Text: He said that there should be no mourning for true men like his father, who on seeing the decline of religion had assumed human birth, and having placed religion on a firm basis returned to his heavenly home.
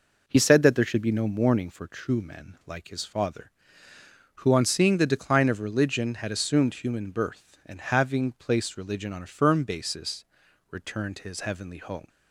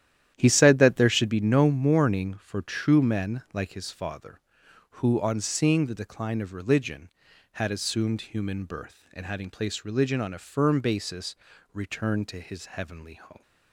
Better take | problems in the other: first | starts louder than the rest; strong; until 1.4 s; 11 dB // pauses between "basis" and "returned"; at 11.3 s; 0.38 s long; noticeable in the first

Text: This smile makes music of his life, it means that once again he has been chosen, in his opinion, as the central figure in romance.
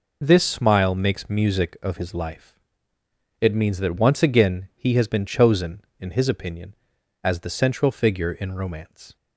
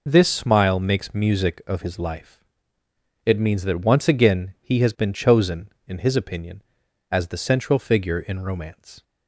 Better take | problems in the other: neither | none

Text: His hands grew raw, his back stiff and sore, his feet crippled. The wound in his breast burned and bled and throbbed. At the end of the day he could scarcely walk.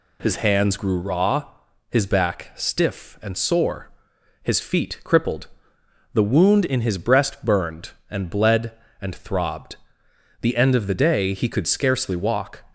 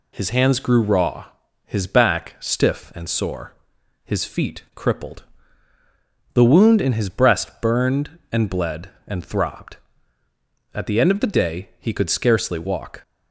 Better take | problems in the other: second | skips "At"; at 10.0 s

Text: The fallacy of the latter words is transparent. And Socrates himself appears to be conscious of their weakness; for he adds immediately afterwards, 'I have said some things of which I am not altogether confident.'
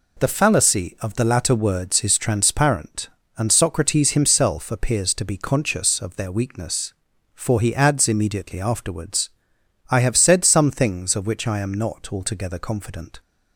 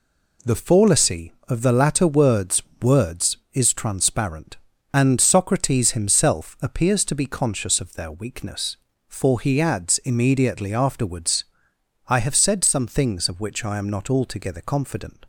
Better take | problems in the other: first | says "words" twice; at 2.8 s

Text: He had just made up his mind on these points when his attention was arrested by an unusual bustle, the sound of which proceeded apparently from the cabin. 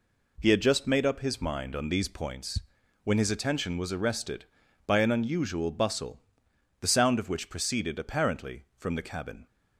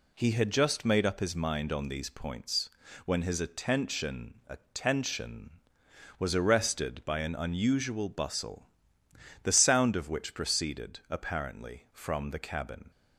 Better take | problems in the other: first | pauses between "points" and "when"; slight; at 2.7 s; 0.34 s long; also in the first // says "attention" twice; at 4.4 s

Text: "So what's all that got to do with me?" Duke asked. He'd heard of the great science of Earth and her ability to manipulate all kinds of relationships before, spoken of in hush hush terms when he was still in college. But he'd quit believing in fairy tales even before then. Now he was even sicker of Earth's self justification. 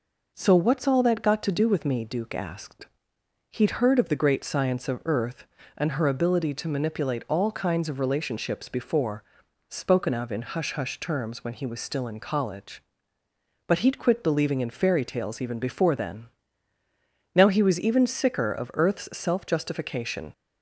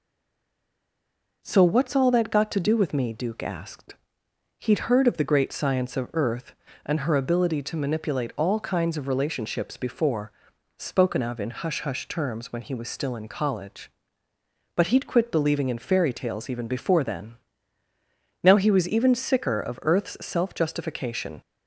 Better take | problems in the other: first | stays silent before the first word; noticeable; until 1.4 s; 1.4 s long

